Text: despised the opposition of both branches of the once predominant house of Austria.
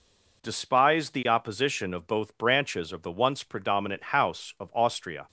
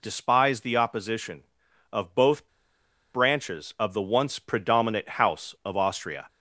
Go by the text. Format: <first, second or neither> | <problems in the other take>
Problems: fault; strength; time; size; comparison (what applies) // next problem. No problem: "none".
first | pauses between "both" and "branches"; noticeable; at 2.4 s; 0.66 s long